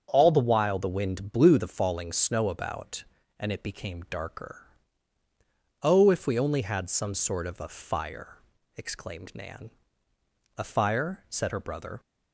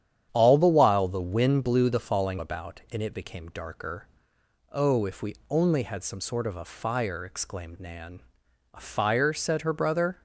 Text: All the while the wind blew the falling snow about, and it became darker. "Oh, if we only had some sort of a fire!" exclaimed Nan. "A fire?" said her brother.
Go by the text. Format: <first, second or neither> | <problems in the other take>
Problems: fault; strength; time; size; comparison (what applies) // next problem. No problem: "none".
first | starts louder than the rest; strong; until 1.3 s; 9.5 dB; also in the first // skips "snow"; at 2.3 s // pauses between "we" and "only"; slight; at 5.3 s; 0.16 s long